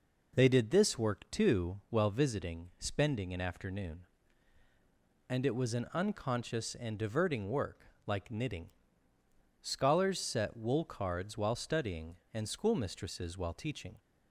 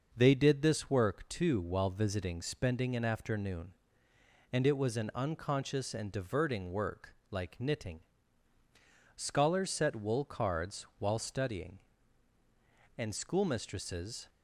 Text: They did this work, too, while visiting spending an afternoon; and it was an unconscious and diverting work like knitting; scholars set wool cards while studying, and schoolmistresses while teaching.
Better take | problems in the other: first | pauses between "work" and "like"; slight; at 7.1 s; 0.16 s long; slight in the first // stops before "while teaching"; at 14.2 s

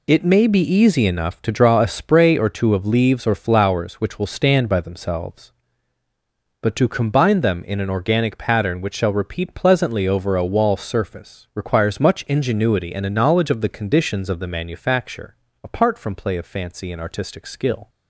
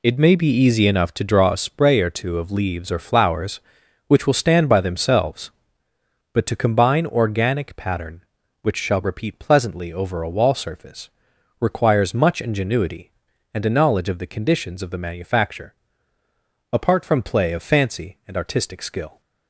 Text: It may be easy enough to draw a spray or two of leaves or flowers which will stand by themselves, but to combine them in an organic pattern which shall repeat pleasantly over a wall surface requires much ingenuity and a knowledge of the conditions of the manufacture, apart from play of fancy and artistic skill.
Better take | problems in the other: first | skips "them in an"; at 7.0 s // pauses between "surface" and "requires"; noticeable; at 11.1 s; 0.48 s long

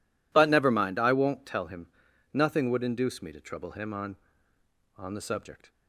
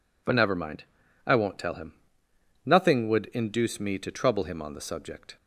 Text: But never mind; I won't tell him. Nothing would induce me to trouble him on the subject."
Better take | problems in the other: second | says "on" twice; at 4.9 s

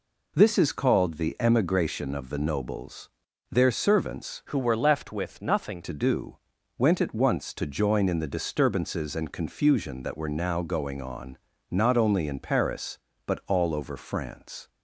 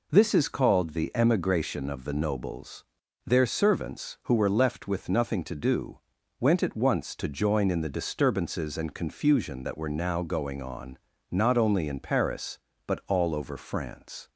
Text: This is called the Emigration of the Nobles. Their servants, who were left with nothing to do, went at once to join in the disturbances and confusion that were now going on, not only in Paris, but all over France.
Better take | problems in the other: second | changes voice from "who" to "nothing"; from 4.4 to 5.7 s; 1.3 s long

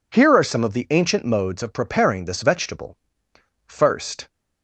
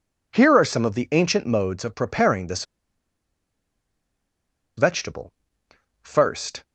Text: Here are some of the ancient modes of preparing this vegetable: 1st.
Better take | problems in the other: first | pauses between "this" and "vegetable"; strong; at 2.6 s; 2.1 s long

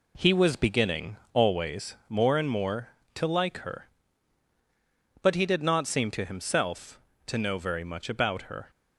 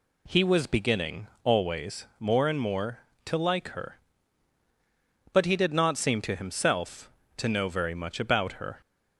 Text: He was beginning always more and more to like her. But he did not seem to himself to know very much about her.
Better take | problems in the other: second | gets quieter; noticeable; throughout; 5.5 dB // pauses between "beginning" and "always"; slight; at 1.1 s; 0.16 s long; slight in the second

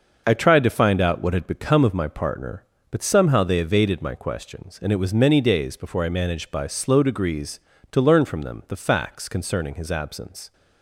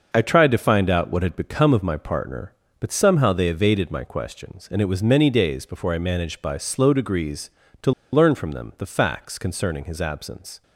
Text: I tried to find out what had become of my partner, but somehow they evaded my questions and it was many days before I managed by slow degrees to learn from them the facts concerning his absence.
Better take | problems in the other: first | pauses between "to" and "learn"; slight; at 7.9 s; 0.22 s long

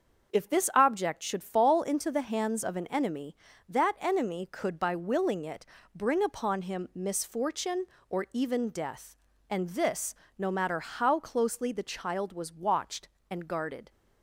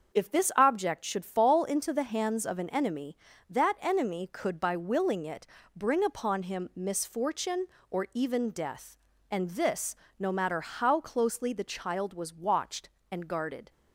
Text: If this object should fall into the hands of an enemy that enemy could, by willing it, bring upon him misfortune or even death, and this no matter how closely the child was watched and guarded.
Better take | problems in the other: neither | starts louder than the rest; the same in both // pauses between "this" and "no"; slight; the same in both

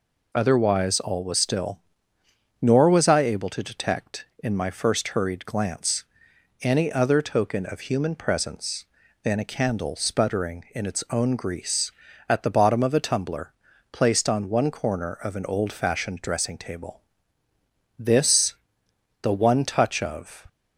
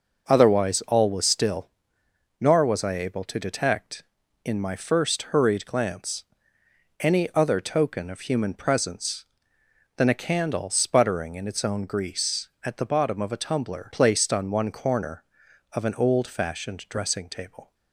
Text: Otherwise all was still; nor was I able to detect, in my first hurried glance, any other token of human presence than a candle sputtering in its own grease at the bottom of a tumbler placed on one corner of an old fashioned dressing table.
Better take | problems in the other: second | pauses between "tumbler" and "placed"; at 13.5 s; 0.40 s long // goes on to say "This the one touch of"; strong; from 17.9 s on; 2.5 s long

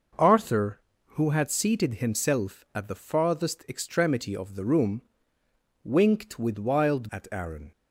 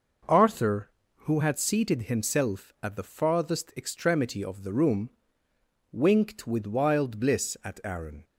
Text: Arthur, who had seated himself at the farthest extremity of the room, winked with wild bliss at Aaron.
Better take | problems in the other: second | skips "bliss"; at 7.1 s

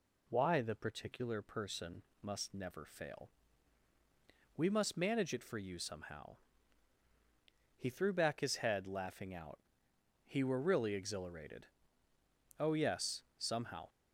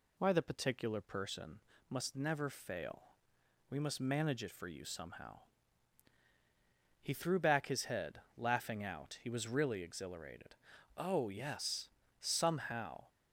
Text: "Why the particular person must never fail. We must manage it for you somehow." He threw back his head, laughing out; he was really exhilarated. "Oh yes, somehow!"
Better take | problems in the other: second | pauses between "person" and "must"; slight; at 2.0 s; 0.20 s long; slight in the second // says "were" for "was"; at 10.4 s

